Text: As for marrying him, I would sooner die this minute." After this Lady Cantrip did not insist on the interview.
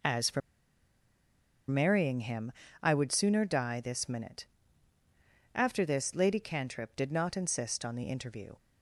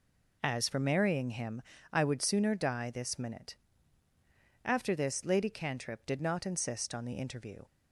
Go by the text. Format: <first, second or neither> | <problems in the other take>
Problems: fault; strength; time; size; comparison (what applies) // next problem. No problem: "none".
second | pauses between "for" and "marrying"; strong; at 0.4 s; 1.2 s long